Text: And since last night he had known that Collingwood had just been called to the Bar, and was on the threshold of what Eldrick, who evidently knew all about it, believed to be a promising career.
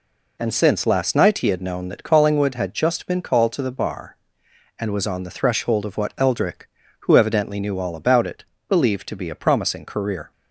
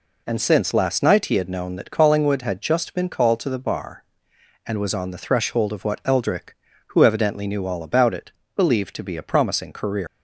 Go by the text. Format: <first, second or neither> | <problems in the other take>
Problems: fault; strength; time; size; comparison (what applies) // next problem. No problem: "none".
first | leaves "career" unfinished; at 10.0 s; 115 ms